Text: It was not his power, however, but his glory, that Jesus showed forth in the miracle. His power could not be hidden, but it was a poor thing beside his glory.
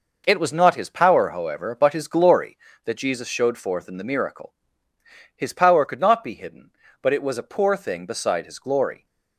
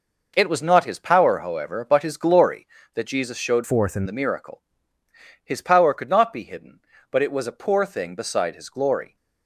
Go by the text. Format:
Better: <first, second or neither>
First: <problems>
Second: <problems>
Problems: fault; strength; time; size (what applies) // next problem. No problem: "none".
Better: first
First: none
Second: changes voice from "forth" to "in"; from 3.6 to 4.0 s; 0.4 s long